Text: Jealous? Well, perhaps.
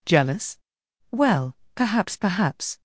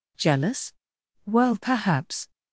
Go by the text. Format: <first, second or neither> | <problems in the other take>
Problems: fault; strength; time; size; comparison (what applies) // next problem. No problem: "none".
second | says "perhaps" twice; at 2.1 s